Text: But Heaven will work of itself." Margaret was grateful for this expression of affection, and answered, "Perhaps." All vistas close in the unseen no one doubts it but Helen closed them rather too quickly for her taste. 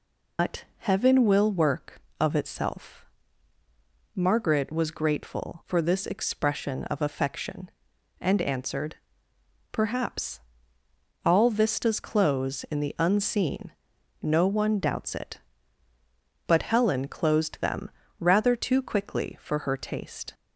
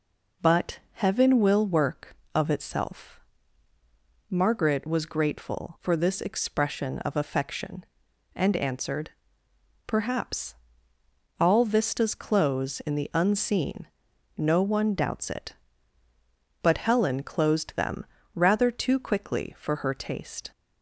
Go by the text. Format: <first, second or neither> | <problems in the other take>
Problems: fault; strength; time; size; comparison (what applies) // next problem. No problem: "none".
second | loses the start of "But"; at 0.3 s; 125 ms // pauses between "unseen" and "no"; noticeable; at 13.7 s; 0.50 s long; noticeable in the second // pauses between "them" and "rather"; slight; at 17.8 s; 0.30 s long; slight in the second